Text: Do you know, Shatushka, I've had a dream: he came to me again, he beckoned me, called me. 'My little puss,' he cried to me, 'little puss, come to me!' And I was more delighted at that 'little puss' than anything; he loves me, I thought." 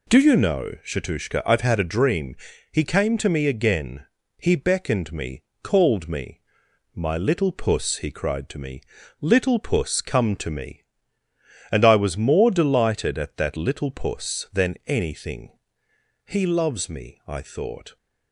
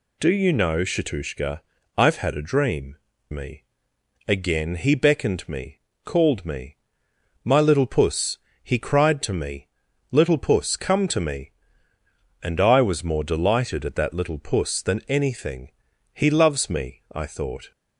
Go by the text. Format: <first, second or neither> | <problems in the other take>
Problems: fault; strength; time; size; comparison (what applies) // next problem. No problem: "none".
first | skips "he came to"; at 3.1 s // pauses between "me" and "again"; noticeable; at 3.6 s; 0.64 s long